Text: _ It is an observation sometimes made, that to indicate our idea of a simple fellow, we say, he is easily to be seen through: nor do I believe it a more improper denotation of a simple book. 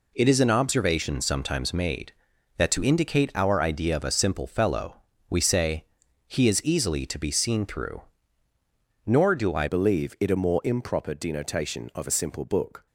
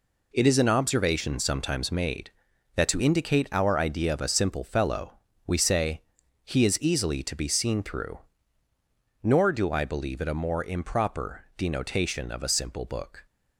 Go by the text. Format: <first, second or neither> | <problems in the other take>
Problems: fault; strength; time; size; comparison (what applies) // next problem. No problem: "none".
second | changes voice at "believe"; from 9.6 s on; 3.2 s long